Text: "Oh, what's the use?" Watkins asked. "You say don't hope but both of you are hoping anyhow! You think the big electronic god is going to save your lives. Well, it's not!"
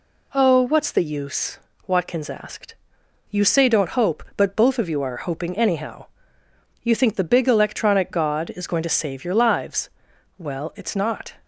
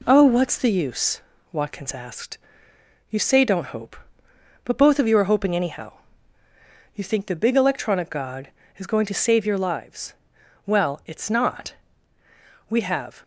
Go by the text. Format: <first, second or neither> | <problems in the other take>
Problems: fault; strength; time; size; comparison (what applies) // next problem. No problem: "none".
first | goes on to say "We have"; from 12.6 s on; 0.54 s long